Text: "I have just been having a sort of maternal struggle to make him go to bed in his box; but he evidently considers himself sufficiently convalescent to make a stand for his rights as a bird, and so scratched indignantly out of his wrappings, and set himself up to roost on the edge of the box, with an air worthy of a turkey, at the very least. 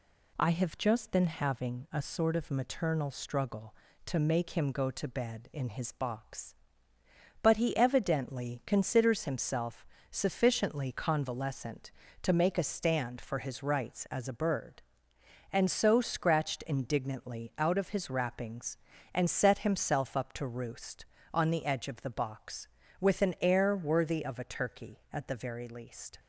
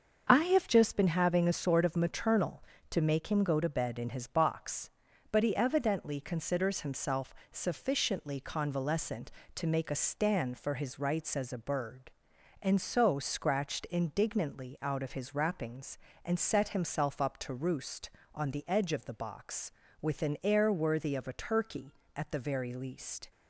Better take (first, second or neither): first